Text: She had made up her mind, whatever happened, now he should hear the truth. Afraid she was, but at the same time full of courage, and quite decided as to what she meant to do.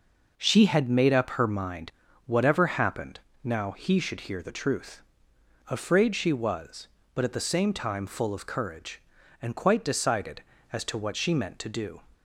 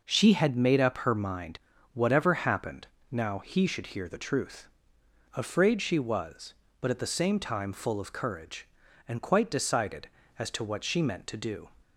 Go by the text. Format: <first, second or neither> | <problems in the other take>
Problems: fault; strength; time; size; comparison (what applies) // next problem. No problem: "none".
neither | none